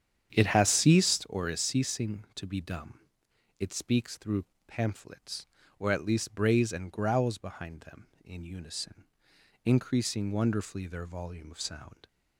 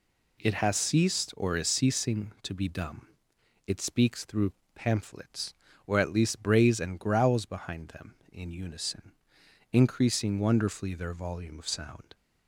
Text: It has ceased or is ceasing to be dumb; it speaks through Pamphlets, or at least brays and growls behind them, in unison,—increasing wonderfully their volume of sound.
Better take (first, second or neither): second